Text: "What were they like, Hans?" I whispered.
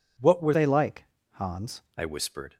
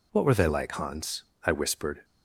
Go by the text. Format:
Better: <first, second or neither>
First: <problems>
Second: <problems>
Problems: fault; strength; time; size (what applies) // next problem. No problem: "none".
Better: second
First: changes voice from "they" to "Hans"; from 0.5 to 1.8 s; 1.3 s long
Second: none